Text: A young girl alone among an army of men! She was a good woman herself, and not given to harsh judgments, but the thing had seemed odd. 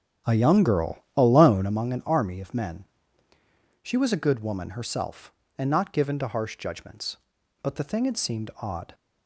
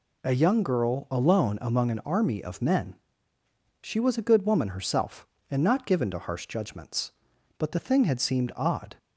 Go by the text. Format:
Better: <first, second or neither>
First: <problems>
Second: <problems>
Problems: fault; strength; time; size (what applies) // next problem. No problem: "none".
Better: second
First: starts louder than the rest; strong; until 1.8 s; 9.5 dB // pauses between "girl" and "alone"; slight; at 0.9 s; 0.18 s long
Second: none